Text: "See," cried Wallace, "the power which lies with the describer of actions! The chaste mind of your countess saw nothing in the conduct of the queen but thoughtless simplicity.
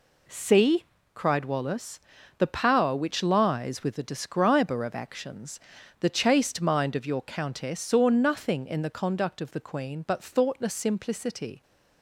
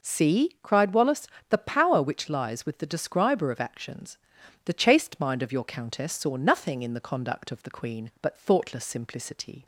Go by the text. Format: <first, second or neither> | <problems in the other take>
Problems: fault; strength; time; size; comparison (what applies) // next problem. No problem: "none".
neither | none